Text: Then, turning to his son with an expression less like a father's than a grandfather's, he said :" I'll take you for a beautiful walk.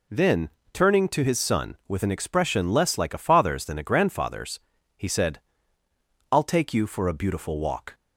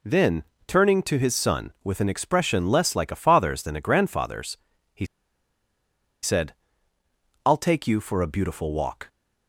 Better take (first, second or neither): first